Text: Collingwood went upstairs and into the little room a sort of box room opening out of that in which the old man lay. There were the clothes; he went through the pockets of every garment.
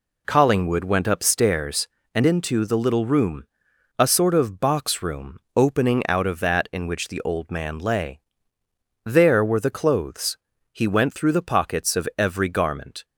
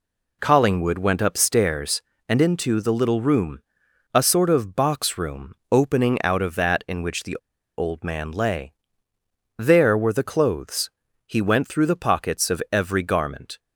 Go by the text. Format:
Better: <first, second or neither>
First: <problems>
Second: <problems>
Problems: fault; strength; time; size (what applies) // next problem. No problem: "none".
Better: first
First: pauses between "room" and "a"; noticeable; at 3.4 s; 0.56 s long // pauses between "room" and "opening"; slight; at 5.3 s; 0.18 s long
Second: pauses between "room" and "a"; noticeable; at 3.5 s; 0.56 s long // pauses between "room" and "opening"; slight; at 5.5 s; 0.18 s long // pauses between "the" and "old"; at 7.3 s; 0.40 s long